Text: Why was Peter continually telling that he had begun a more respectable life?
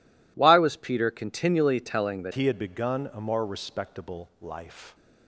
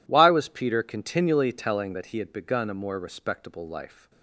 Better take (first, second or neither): second